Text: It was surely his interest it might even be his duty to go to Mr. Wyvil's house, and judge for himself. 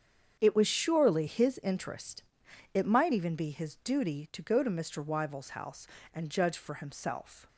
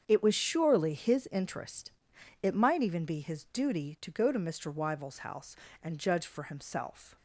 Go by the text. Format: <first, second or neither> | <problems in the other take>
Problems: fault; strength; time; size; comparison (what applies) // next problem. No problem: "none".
neither | starts louder than the rest; strong; the same in both // pauses between "interest" and "it"; noticeable; the same in both